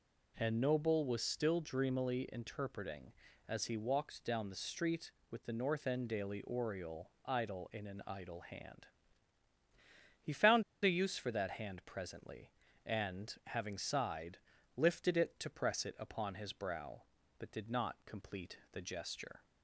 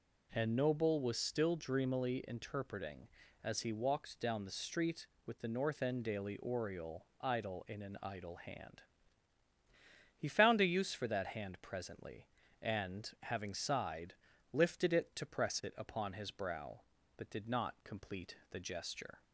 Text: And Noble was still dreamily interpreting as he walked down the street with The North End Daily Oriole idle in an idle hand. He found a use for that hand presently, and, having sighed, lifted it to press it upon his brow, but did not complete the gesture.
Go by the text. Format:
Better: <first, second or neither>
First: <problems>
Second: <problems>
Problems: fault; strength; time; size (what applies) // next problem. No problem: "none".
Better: second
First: pauses between "found" and "a"; slight; at 10.6 s; 0.21 s long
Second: none